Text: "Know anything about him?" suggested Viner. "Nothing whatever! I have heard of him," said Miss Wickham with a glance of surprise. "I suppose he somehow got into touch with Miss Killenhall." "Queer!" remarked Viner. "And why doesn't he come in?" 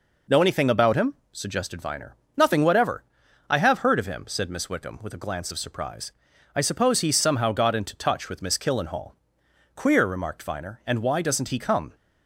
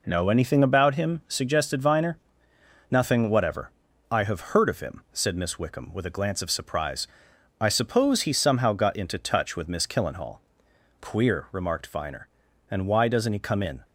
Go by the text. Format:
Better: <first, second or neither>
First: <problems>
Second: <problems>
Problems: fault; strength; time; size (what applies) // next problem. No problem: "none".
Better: second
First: stops before "in"; at 11.9 s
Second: none